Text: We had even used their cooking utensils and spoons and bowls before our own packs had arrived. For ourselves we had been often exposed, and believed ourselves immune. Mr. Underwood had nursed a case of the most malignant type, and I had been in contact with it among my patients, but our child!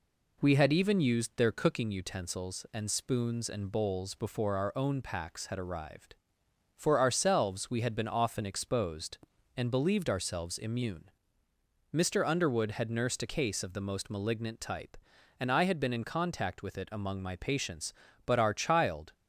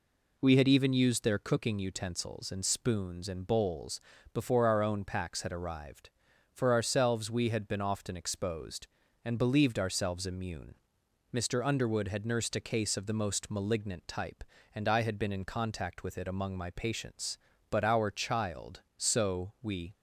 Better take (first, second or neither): first